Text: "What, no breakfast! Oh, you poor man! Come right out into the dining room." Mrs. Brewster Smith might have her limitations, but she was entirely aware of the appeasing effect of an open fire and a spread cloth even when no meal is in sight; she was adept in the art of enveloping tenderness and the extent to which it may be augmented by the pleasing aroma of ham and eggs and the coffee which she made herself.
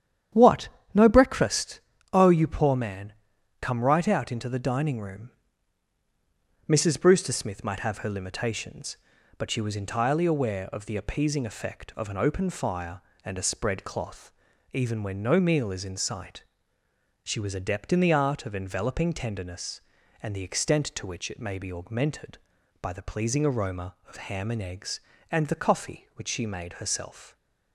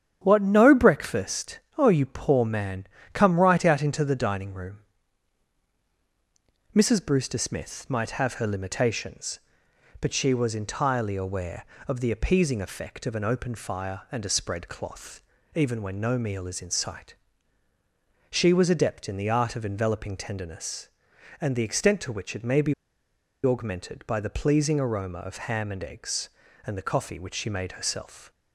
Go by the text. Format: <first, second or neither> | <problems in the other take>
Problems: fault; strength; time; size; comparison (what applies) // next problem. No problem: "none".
first | starts louder than the rest; strong; until 1.2 s; 9 dB; strong in the first // pauses between "cloth" and "even"; slight; at 15.2 s; 0.34 s long; also in the first // pauses between "be" and "augmented"; noticeable; at 22.7 s; 0.72 s long